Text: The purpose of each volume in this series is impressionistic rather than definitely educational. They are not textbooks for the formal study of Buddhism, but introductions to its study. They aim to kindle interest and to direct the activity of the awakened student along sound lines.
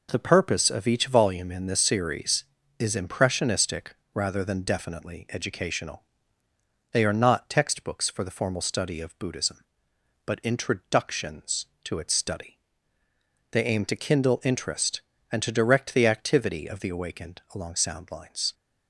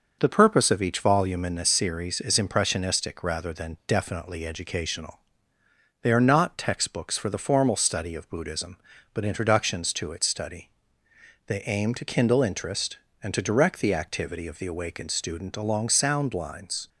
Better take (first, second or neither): second